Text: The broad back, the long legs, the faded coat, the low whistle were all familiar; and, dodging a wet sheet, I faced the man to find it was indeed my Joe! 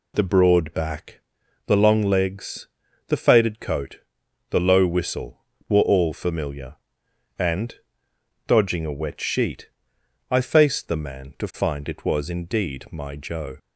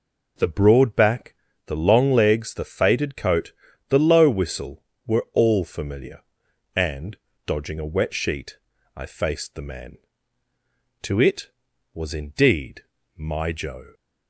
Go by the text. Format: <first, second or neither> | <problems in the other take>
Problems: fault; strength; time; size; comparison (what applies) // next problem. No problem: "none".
first | skips "find"; at 11.2 s // pauses between "indeed" and "my"; slight; at 12.8 s; 0.34 s long